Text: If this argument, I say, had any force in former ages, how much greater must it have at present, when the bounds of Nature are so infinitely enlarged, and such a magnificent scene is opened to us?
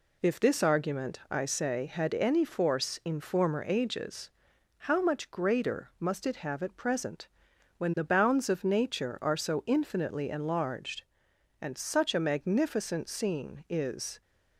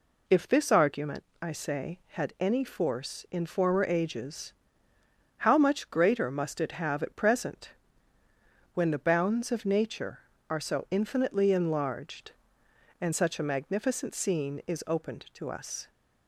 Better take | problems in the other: second | stops before "opened to us"; at 14.2 s

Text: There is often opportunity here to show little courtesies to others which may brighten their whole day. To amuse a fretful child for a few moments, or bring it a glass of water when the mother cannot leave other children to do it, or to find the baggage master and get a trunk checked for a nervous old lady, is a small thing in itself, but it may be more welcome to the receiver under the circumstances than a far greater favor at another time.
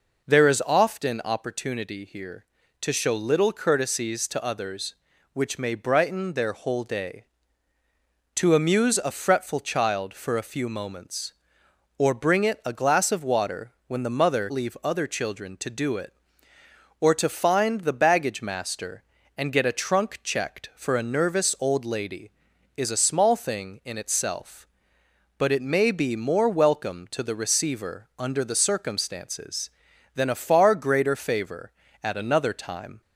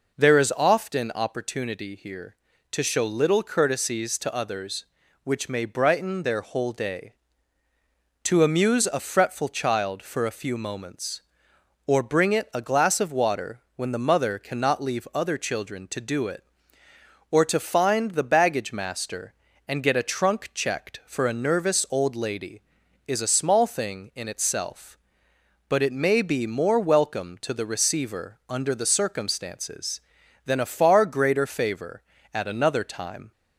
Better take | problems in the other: second | pauses between "water" and "when"; slight; at 13.7 s; 0.16 s long; slight in the second // skips "cannot"; at 14.5 s

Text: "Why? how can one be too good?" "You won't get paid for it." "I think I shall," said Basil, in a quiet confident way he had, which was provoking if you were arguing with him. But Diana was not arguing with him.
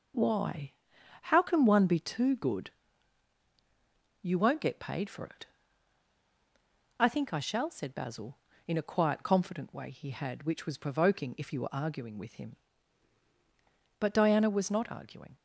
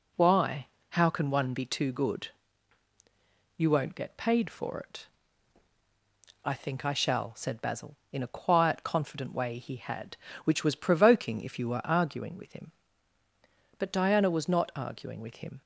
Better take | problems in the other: second | stops before "with him"; at 15.3 s

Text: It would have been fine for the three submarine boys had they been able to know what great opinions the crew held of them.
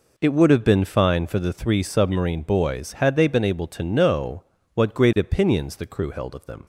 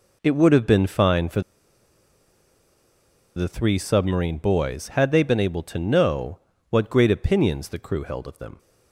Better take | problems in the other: first | pauses between "for" and "the"; strong; at 1.4 s; 1.9 s long // pauses between "know" and "what"; slight; at 6.3 s; 0.28 s long; slight in the first

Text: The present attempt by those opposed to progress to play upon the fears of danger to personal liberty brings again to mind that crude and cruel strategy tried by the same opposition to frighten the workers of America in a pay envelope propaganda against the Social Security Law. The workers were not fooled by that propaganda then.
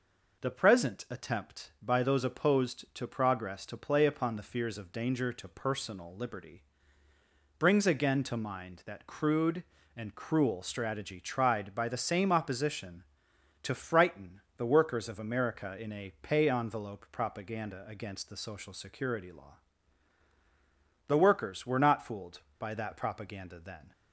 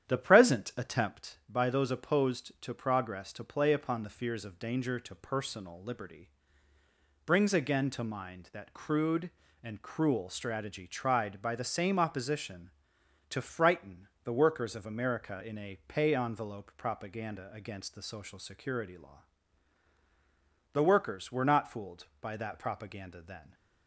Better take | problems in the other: first | starts louder than the rest; strong; until 1.3 s; 10 dB // pauses between "liberty" and "brings"; noticeable; at 6.2 s; 0.96 s long; noticeable in the first // pauses between "frighten" and "the"; slight; at 14.0 s; 0.18 s long; slight in the first

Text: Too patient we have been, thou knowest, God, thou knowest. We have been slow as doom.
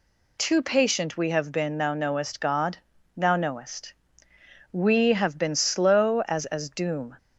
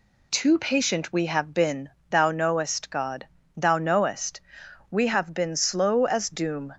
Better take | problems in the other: second | says "as" twice; at 6.4 s

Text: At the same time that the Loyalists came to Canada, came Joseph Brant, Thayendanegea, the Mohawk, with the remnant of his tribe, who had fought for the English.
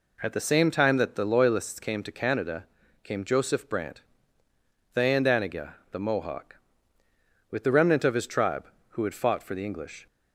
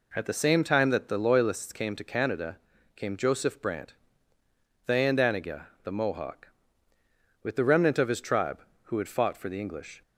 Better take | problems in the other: neither | none

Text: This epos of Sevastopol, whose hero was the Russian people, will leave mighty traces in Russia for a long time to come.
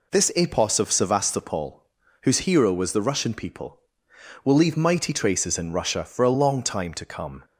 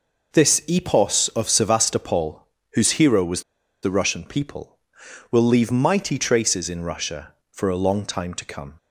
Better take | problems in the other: first | pauses between "was" and "the"; at 3.4 s; 0.41 s long

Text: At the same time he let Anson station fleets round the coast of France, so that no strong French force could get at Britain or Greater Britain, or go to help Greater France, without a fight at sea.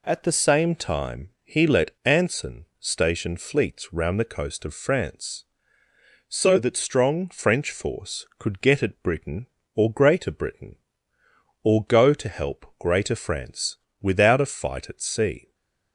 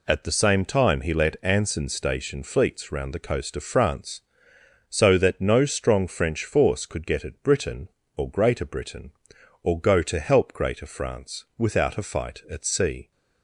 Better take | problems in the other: second | skips "no"; at 6.7 s // stays silent after the last word; slight; from 15.4 s on; 0.5 s long

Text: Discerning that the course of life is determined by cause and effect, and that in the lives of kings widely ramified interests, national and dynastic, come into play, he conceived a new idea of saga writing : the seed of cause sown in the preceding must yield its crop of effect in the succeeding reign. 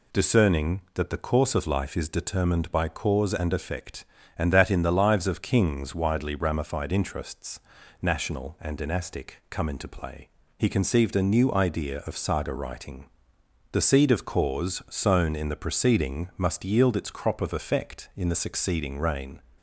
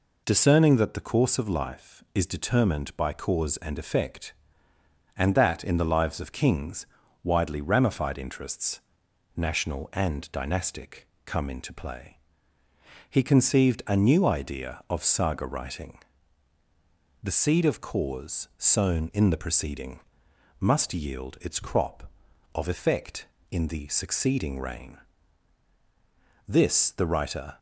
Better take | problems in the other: first | pauses between "kings" and "widely"; slight; at 6.8 s; 0.36 s long // pauses between "preceding" and "must"; noticeable; at 20.0 s; 0.58 s long // goes on to say "This the writer"; noticeable; from 26.4 s on; 1.1 s long

